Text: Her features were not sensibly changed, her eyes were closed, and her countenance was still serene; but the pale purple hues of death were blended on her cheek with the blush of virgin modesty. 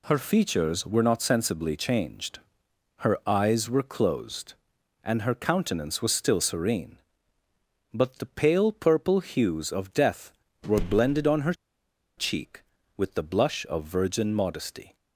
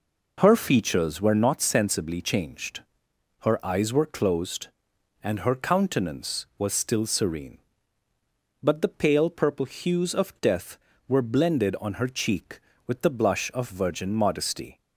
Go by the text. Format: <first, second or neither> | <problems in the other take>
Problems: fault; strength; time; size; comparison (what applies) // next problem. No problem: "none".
second | pauses between "her" and "cheek"; noticeable; at 11.5 s; 0.62 s long